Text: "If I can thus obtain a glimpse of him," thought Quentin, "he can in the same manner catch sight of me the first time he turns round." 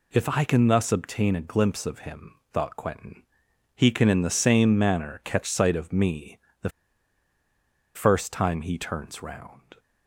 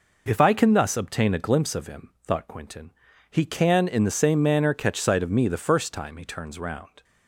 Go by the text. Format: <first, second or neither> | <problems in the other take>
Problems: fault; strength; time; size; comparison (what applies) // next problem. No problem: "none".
second | pauses between "me" and "the"; slight; at 6.3 s; 0.26 s long // pauses between "the" and "first"; strong; at 6.6 s; 1.2 s long